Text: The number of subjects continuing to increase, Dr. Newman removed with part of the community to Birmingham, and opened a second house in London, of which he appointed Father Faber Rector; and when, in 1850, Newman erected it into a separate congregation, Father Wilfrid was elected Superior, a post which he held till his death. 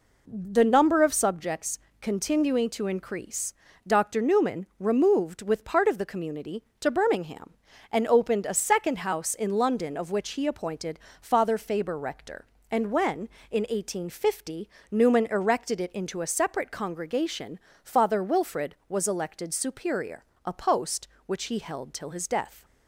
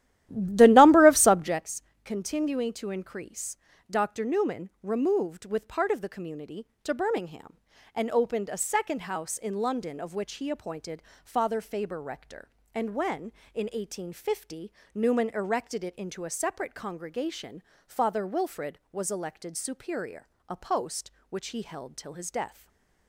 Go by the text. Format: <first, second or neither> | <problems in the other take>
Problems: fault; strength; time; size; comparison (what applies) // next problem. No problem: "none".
first | starts louder than the rest; strong; until 1.7 s; 13.5 dB // pauses between "subjects" and "continuing"; slight; at 1.8 s; 0.22 s long; slight in the first // pauses between "appointed" and "Father"; slight; at 11.0 s; 0.22 s long; slight in the first // stays silent after the last word; slight; from 22.4 s on; 0.6 s long